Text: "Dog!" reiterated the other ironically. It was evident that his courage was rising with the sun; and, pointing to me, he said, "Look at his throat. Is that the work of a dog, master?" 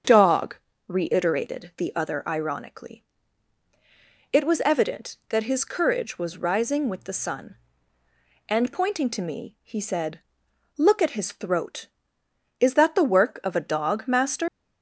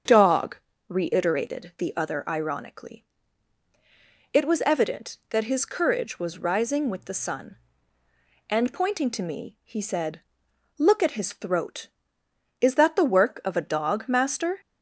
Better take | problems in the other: second | starts louder than the rest; strong; until 1.3 s; 7.5 dB; strong in the second // leaves "master" unfinished; at 14.4 s; 115 ms

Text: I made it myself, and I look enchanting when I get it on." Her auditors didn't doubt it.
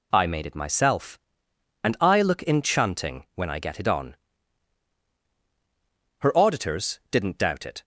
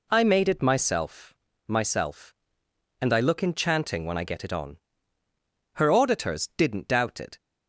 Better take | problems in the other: first | says "myself" twice; at 1.6 s

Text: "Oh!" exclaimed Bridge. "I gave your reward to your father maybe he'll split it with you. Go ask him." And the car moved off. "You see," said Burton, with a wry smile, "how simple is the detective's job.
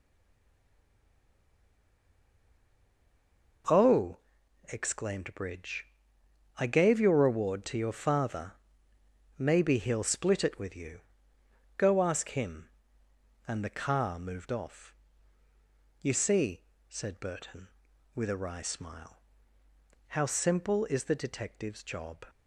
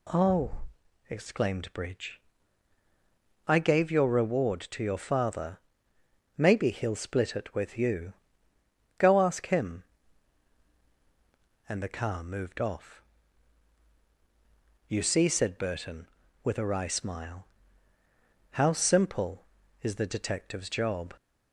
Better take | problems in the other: second | stays silent before the first word; strong; until 3.6 s; 3.6 s long // pauses between "father" and "maybe"; noticeable; at 8.5 s; 0.86 s long; noticeable in the second

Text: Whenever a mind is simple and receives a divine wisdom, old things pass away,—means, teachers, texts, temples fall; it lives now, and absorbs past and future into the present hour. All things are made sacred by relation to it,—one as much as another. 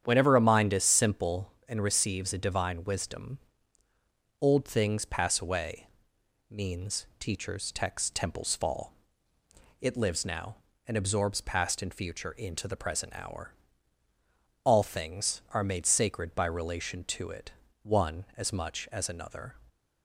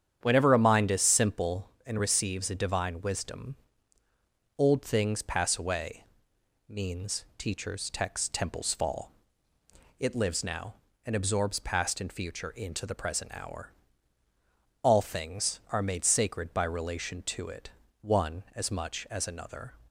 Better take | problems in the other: neither | starts louder than the rest; strong; the same in both

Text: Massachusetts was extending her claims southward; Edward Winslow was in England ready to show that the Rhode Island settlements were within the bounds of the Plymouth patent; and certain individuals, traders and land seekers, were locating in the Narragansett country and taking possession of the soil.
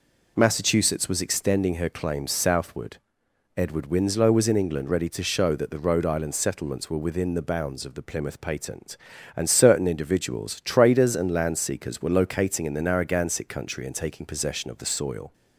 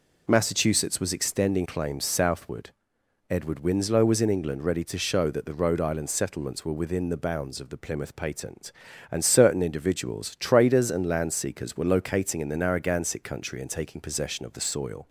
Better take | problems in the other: first | skips "her"; at 1.6 s

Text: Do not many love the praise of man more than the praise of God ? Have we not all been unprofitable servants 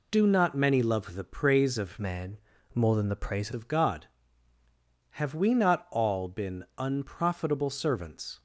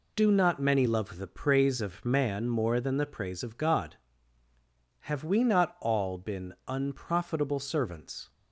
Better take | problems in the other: second | changes voice from "man" to "praise"; from 2.0 to 3.5 s; 1.5 s long // pauses between "man" and "more"; slight; at 2.3 s; 0.34 s long

